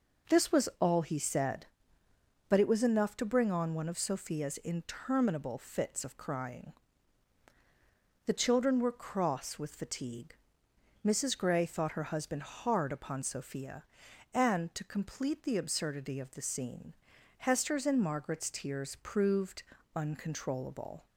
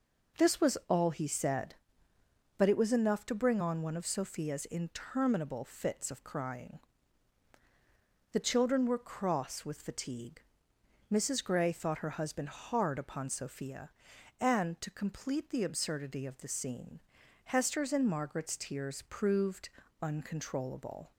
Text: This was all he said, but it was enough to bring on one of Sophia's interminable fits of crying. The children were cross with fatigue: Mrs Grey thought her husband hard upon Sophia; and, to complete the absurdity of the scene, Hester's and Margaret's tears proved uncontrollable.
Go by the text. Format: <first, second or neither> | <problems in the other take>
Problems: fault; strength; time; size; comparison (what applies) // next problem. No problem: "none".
neither | pauses between "proved" and "uncontrollable"; slight; the same in both